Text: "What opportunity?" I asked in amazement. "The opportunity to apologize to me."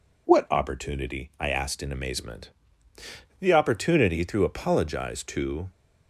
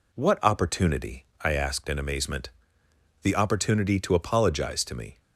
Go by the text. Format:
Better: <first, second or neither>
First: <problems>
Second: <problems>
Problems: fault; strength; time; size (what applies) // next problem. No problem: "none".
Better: second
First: stops before "me"; at 5.6 s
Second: none